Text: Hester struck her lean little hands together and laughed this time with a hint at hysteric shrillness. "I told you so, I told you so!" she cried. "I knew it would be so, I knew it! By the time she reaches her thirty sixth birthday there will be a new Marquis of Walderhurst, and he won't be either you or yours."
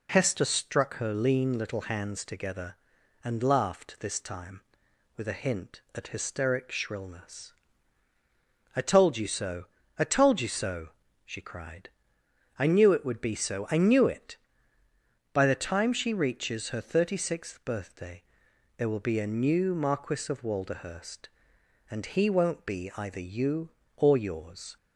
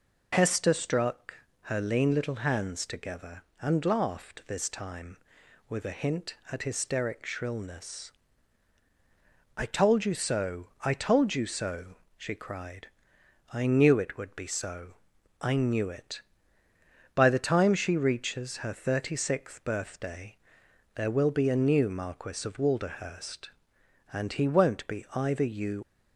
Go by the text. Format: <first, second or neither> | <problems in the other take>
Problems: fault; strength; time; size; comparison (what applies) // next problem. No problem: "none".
first | pauses between "struck" and "her"; slight; at 1.3 s; 0.26 s long // pauses between "birthday" and "there"; noticeable; at 20.3 s; 0.60 s long; noticeable in the first // stops before "or yours"; at 25.8 s